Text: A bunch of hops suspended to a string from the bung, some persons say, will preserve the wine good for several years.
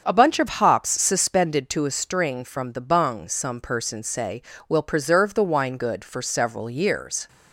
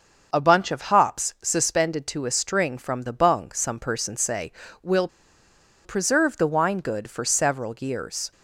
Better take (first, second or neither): first